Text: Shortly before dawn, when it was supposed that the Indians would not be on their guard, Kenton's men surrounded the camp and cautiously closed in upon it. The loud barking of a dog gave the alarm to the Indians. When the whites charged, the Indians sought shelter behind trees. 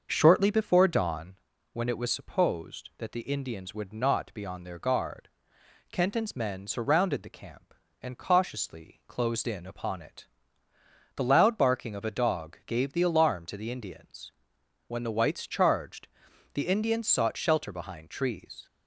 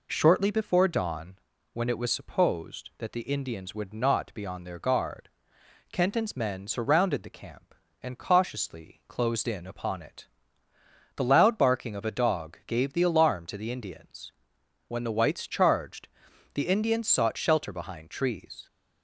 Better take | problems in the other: second | starts louder than the rest; until 1.3 s; 6.5 dB

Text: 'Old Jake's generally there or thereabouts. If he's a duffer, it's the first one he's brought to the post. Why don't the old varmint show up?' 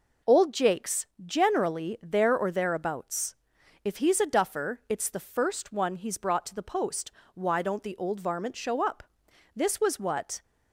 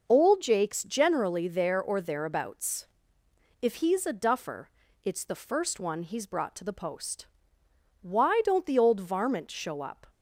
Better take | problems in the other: second | pauses between "Jake's" and "generally"; slight; at 1.0 s; 0.18 s long // goes on to say "This was what"; noticeable; from 9.5 s on; 0.88 s long

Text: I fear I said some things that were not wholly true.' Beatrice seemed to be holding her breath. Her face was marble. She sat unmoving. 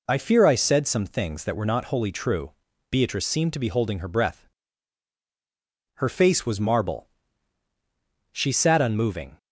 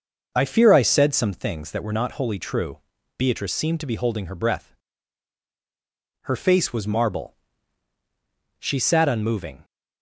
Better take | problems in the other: first | starts louder than the rest; noticeable; until 1.4 s; 6 dB

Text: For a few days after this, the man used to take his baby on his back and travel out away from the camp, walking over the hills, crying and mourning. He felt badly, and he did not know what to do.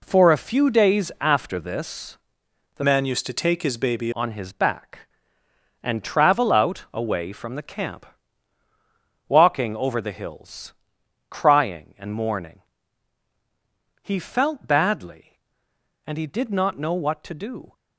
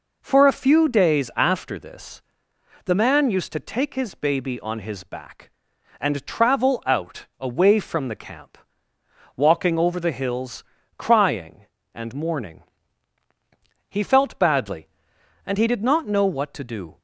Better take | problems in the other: second | changes voice from "man" to "baby"; from 2.8 to 4.1 s; 1.3 s long

